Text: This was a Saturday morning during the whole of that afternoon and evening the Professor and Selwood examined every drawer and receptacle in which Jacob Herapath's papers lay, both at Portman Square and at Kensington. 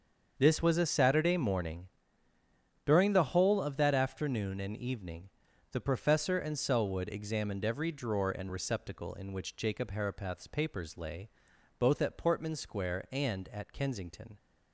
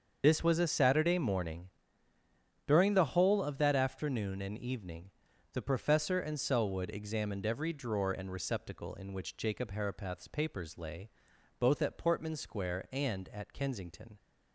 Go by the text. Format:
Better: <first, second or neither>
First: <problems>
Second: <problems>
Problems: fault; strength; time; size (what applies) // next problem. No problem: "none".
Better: first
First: starts louder than the rest; until 1.3 s; 7 dB // pauses between "morning" and "during"; noticeable; at 1.8 s; 0.98 s long // pauses between "evening" and "the"; at 5.3 s; 0.42 s long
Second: loses the start of "This"; at 0.2 s; 45 ms // starts louder than the rest; until 1.2 s; 7 dB // pauses between "morning" and "during"; noticeable; at 1.6 s; 0.98 s long // pauses between "evening" and "the"; at 5.1 s; 0.42 s long